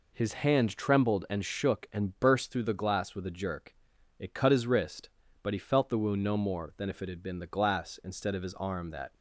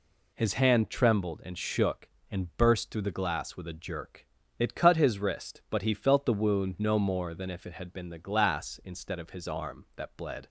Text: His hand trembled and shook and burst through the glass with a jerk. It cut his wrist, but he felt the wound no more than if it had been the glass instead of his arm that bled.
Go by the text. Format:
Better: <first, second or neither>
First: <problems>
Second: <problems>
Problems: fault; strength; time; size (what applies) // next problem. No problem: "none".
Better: second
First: stops before "bled"; at 9.1 s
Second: none